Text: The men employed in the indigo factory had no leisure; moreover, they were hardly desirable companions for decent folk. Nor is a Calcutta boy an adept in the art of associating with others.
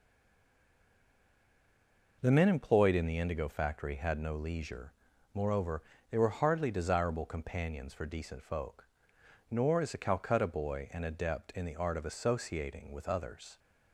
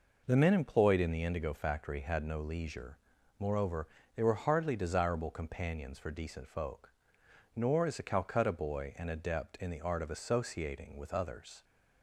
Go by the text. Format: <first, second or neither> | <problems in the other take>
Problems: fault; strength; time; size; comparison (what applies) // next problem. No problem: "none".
second | stays silent before the first word; until 2.2 s; 2.2 s long